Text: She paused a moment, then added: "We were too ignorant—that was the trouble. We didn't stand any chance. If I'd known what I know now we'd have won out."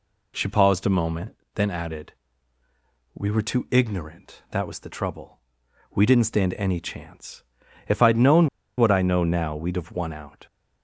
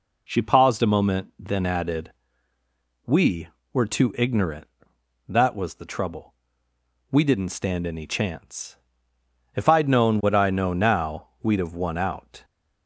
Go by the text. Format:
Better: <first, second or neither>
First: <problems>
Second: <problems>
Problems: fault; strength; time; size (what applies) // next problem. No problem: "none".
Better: second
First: pauses between "known" and "what"; slight; at 8.4 s; 0.29 s long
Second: none